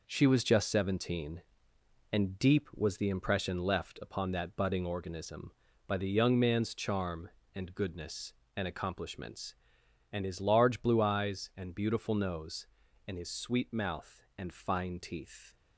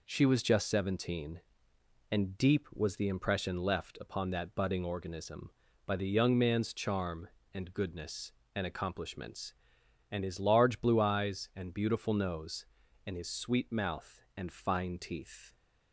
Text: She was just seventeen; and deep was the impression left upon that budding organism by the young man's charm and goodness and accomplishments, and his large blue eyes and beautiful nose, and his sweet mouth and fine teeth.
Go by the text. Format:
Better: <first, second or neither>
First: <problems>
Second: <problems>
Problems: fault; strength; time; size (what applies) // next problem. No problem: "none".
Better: second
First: gets quieter; throughout; 7 dB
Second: none